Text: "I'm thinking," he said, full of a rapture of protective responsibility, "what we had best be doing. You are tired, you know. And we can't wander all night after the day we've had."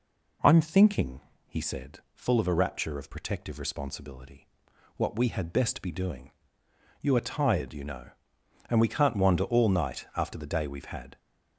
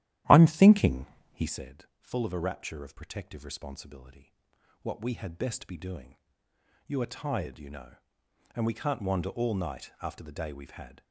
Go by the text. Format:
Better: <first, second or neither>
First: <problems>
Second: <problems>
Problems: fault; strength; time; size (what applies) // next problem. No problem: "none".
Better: first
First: none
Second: starts louder than the rest; strong; until 1.6 s; 12.5 dB